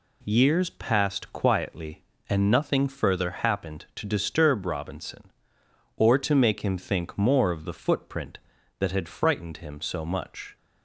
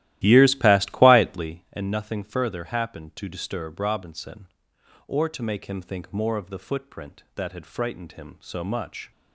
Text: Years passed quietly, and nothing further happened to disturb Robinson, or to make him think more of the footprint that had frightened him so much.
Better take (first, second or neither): first